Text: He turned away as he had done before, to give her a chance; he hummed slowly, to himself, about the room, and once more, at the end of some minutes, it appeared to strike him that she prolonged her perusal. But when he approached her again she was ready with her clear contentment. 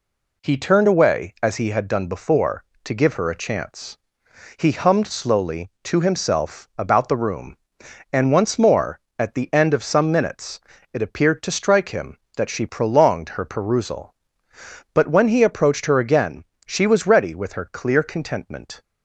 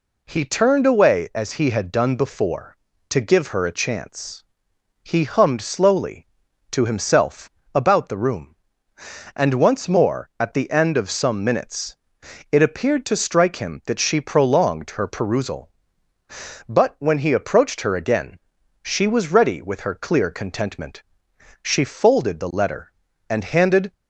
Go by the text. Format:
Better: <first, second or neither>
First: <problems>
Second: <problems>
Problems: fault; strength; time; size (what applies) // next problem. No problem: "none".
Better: first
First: pauses between "again" and "she"; slight; at 16.4 s; 0.22 s long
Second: pauses between "again" and "she"; at 18.3 s; 0.42 s long // goes on to say "She folded the letter and handed"; strong; from 21.6 s on; 2.2 s long